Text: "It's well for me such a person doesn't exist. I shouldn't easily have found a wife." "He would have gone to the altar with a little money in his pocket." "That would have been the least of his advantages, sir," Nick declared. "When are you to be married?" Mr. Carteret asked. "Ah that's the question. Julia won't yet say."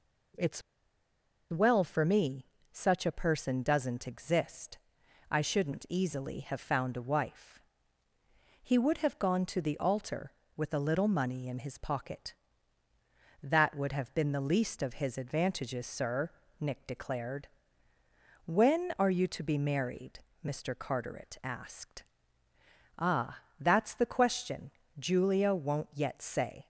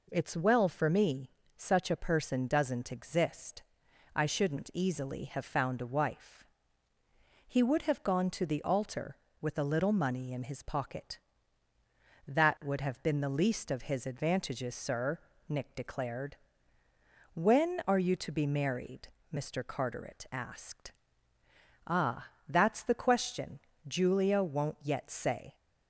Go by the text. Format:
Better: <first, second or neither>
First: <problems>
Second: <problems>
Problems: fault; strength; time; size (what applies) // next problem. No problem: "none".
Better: second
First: pauses between "It's" and "well"; noticeable; at 0.6 s; 0.89 s long // pauses between "me" and "such"; slight; at 2.4 s; 0.28 s long // pauses between "Ah" and "that's"; slight; at 23.4 s; 0.18 s long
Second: pauses between "me" and "such"; slight; at 1.2 s; 0.28 s long // pauses between "Ah" and "that's"; slight; at 22.2 s; 0.18 s long